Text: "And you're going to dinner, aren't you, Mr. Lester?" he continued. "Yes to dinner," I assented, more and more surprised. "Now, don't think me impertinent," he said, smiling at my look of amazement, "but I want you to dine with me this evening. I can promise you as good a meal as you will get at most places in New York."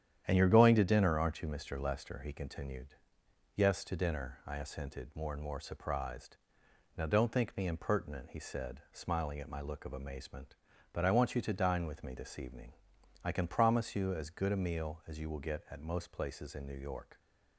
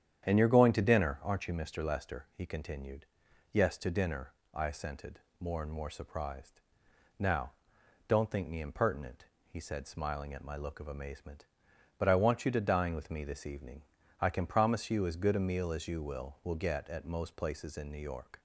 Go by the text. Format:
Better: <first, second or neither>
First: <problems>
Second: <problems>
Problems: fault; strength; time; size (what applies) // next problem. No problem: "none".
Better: first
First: starts louder than the rest; strong; until 1.2 s; 9.5 dB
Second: starts louder than the rest; strong; until 1.3 s; 9 dB // says "will" twice; at 16.4 s